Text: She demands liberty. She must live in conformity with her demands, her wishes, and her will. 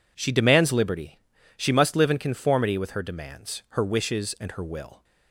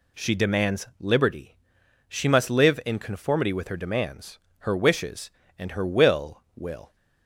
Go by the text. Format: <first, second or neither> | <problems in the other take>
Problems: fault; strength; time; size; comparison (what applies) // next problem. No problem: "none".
first | says "will" twice; at 6.5 s